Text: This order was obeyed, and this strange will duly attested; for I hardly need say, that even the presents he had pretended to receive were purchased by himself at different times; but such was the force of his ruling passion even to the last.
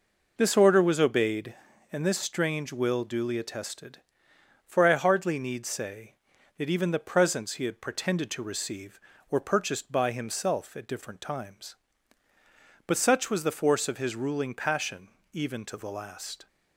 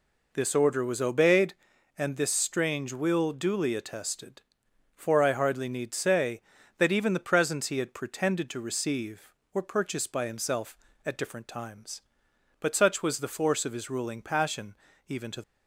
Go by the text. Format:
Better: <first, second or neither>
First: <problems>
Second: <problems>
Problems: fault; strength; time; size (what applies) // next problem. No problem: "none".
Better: first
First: pauses between "passion" and "even"; slight; at 15.0 s; 0.26 s long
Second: pauses between "passion" and "even"; slight; at 14.7 s; 0.32 s long // stops before "the last"; at 15.4 s